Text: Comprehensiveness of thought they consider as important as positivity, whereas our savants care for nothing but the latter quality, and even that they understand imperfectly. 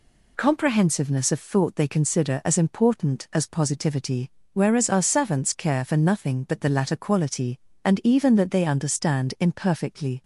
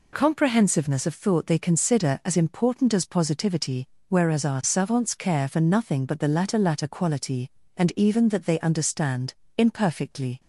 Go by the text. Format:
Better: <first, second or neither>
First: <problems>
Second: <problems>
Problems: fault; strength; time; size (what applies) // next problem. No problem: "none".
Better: first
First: none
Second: says "latter" twice; at 6.5 s // pauses between "understand" and "imperfectly"; slight; at 9.3 s; 0.24 s long